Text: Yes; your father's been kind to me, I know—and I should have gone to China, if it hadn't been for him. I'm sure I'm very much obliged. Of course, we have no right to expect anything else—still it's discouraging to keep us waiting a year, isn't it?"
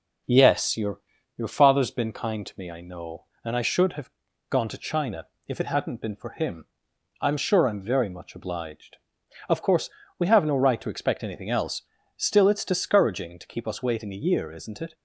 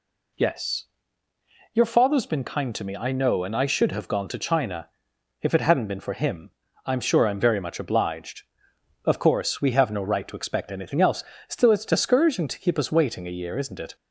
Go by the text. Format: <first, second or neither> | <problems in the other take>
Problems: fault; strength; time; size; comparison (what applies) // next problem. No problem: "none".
second | says "your" twice; at 1.3 s // pauses between "have" and "gone"; at 4.0 s; 0.38 s long